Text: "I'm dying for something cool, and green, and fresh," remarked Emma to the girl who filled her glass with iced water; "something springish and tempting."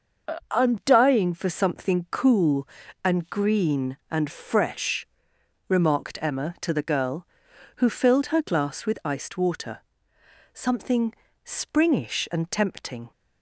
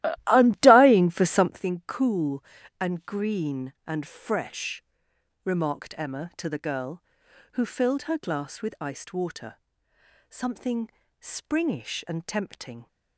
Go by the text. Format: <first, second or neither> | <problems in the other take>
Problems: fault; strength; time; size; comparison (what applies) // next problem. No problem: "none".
first | starts louder than the rest; strong; until 1.6 s; 15 dB // pauses between "something" and "springish"; slight; at 10.8 s; 0.32 s long; slight in the first